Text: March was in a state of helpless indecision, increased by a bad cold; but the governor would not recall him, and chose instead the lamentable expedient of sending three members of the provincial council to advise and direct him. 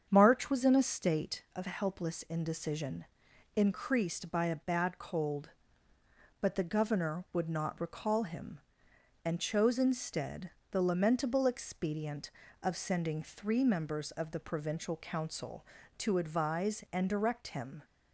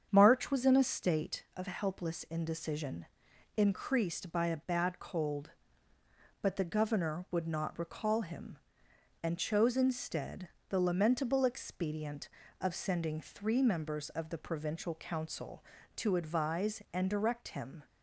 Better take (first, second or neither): neither